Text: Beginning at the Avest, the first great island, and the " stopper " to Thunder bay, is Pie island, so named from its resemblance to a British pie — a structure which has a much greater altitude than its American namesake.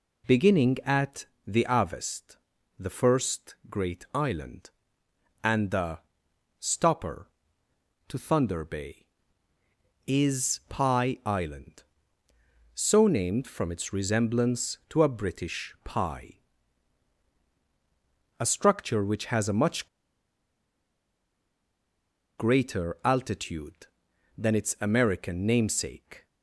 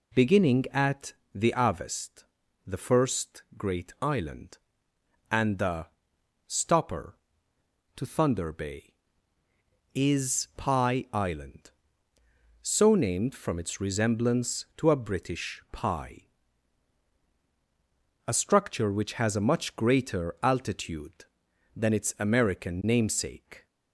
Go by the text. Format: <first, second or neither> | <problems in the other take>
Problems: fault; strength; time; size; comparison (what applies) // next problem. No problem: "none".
second | pauses between "at" and "the"; slight; at 1.2 s; 0.18 s long; slight in the second // pauses between "first" and "great"; slight; at 3.5 s; 0.16 s long; slight in the second // pauses between "much" and "greater"; strong; at 19.8 s; 2.5 s long